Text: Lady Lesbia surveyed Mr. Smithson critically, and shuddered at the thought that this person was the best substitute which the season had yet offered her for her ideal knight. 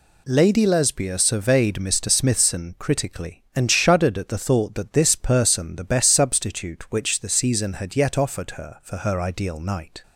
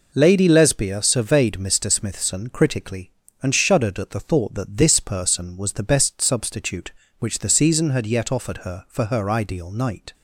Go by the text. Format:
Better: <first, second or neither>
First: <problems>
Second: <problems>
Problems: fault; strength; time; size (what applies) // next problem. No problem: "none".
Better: second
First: skips "was"; at 5.7 s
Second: none